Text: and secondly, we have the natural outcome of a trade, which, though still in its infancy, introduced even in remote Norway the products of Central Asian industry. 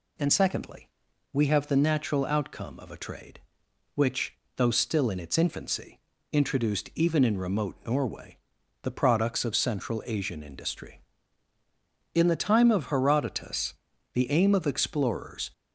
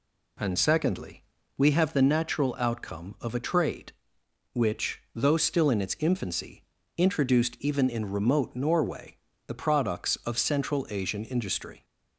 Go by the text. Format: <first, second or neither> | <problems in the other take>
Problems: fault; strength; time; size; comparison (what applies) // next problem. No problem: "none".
second | pauses between "Norway" and "the"; noticeable; at 8.3 s; 0.46 s long; slight in the second // goes on to say "In the time of Herodotus the aim of explorers"; strong; from 12.1 s on; 3.3 s long